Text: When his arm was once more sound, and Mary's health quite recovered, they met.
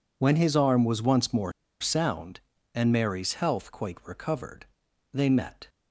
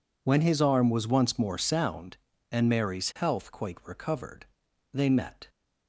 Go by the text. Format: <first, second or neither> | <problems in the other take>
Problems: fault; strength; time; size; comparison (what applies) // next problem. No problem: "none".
second | pauses between "more" and "sound"; slight; at 1.5 s; 0.28 s long